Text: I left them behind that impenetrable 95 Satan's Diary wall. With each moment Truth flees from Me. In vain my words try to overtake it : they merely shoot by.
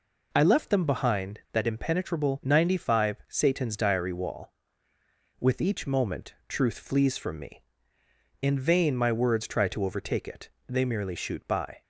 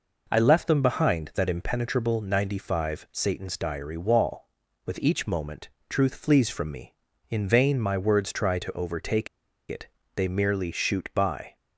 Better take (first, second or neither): first